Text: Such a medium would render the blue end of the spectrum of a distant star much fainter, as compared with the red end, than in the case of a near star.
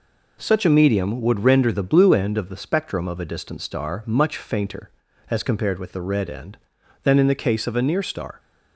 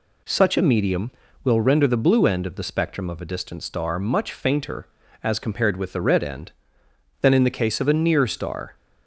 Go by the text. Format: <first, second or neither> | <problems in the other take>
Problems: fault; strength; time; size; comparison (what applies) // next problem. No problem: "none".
first | says "will" for "would"; at 1.4 s